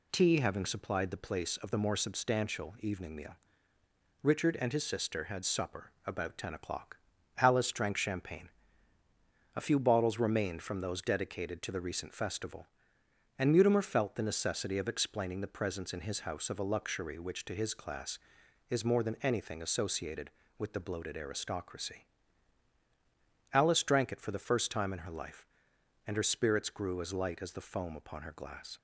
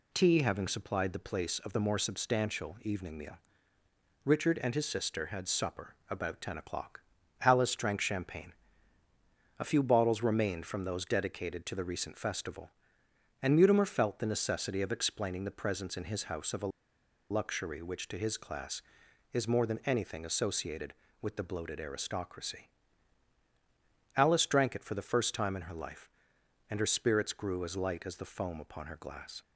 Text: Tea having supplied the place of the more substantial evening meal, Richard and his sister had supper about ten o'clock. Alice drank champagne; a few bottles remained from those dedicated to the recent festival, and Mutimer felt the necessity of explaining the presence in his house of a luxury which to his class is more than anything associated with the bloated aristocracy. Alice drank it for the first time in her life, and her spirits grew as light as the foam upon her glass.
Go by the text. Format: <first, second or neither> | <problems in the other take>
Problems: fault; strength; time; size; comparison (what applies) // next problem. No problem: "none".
first | pauses between "a" and "luxury"; noticeable; at 16.7 s; 0.60 s long